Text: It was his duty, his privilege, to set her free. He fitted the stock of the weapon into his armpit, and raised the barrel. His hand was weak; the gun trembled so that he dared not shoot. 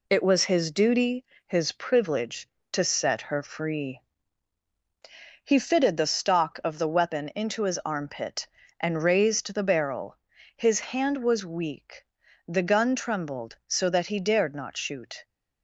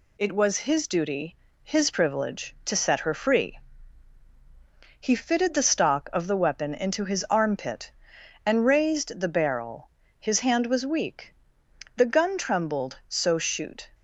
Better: first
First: none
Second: skips "that he dared not"; at 13.3 s

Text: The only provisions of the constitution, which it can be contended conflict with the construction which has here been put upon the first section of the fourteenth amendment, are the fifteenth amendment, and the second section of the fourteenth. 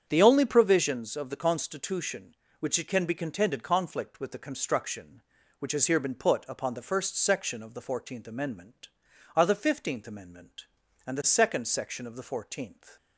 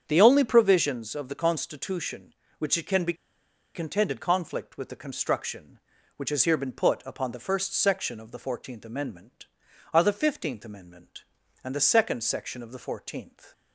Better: first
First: starts louder than the rest; strong; until 1.0 s; 8 dB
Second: starts louder than the rest; strong; until 1.0 s; 8 dB // pauses between "be" and "contended"; noticeable; at 3.1 s; 0.61 s long

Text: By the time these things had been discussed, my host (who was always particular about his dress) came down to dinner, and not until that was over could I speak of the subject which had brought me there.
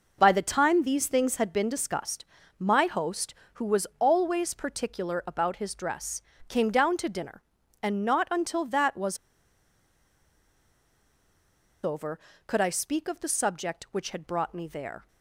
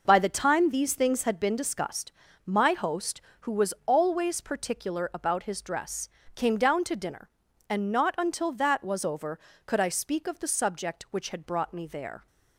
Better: second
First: pauses between "was" and "over"; strong; at 9.1 s; 2.6 s long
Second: none

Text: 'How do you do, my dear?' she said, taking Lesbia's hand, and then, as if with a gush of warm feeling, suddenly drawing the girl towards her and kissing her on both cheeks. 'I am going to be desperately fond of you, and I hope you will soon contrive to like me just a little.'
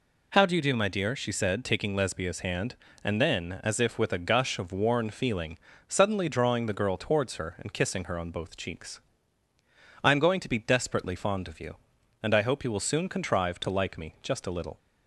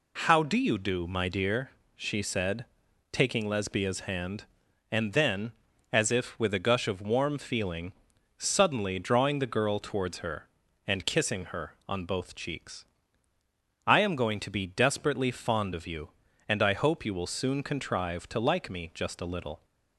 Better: second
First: says "worn" for "warm"; at 4.7 s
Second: none

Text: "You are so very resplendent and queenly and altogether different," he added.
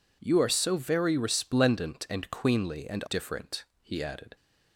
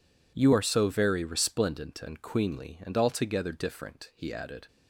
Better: second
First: skips "altogether"; at 3.0 s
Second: none

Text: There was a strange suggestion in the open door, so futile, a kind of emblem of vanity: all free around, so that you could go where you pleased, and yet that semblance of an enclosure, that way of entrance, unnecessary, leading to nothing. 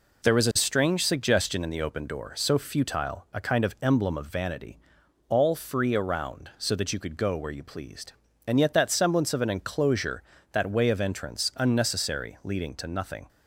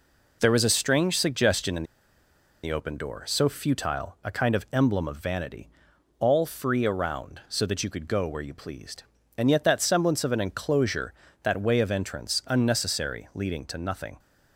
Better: first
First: none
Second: pauses between "in" and "the"; noticeable; at 1.8 s; 0.80 s long

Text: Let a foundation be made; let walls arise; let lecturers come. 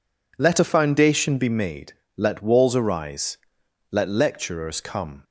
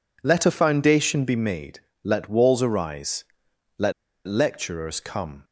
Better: first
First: none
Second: pauses between "let" and "lecturers"; slight; at 3.9 s; 0.35 s long

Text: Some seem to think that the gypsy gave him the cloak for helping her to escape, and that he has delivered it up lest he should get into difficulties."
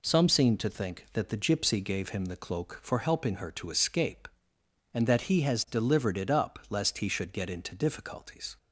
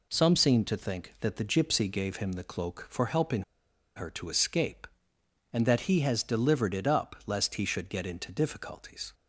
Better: first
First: none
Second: pauses between "helping" and "her"; noticeable; at 3.4 s; 0.53 s long

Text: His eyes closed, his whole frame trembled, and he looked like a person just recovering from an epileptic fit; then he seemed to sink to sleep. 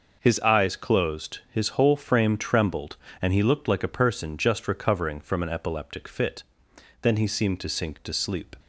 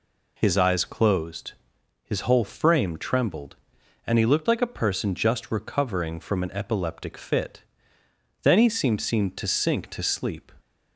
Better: first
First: none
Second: says "seemed" twice; at 9.0 s

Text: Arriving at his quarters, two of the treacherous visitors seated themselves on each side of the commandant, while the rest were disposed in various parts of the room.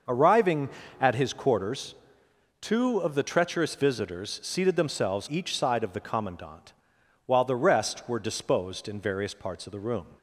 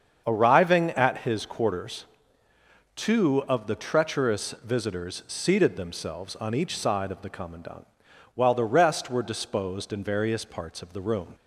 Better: second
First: starts louder than the rest; noticeable; until 1.3 s; 6 dB // skips "on"; at 5.2 s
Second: starts louder than the rest; strong; until 1.2 s; 7 dB

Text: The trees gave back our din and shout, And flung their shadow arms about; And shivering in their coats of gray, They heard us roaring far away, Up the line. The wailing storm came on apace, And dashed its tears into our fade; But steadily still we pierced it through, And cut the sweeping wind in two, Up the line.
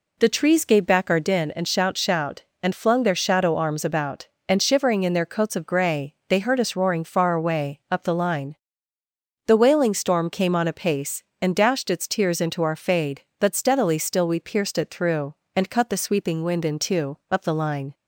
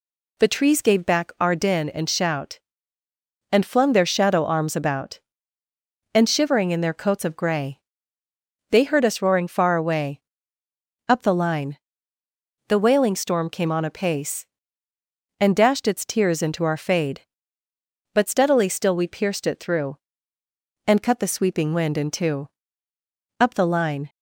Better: second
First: says "shout" twice; at 1.9 s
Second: none

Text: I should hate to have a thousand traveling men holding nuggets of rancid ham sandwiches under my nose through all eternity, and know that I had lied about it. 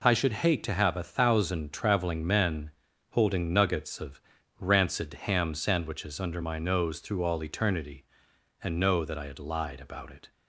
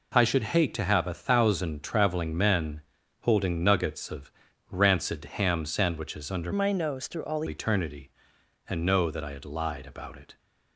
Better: first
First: pauses between "men" and "holding"; at 2.7 s; 0.38 s long // pauses between "of" and "rancid"; at 4.2 s; 0.37 s long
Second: pauses between "men" and "holding"; at 2.8 s; 0.38 s long // pauses between "of" and "rancid"; at 4.3 s; 0.38 s long // changes voice from "my" to "all"; from 6.5 to 7.4 s; 0.9 s long

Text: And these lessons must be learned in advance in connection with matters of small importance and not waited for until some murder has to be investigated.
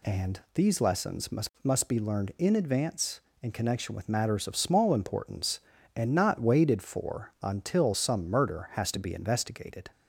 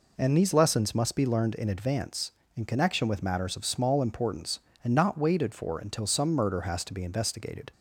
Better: second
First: says "must" twice; at 1.6 s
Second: none

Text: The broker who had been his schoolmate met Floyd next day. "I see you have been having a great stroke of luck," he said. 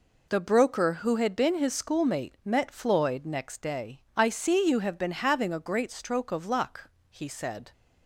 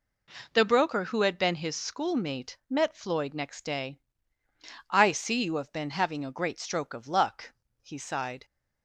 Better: first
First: none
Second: says "sighed" for "said"; at 7.9 s

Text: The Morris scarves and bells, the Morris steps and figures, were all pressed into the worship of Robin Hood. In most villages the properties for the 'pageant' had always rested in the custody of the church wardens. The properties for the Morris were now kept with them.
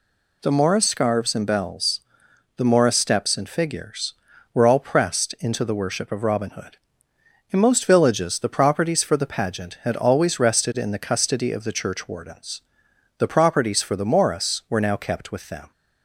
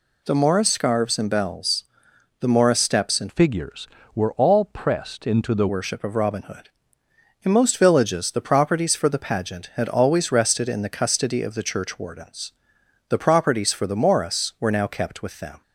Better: first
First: none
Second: changes voice from "figures" to "the"; from 3.2 to 5.6 s; 2.4 s long

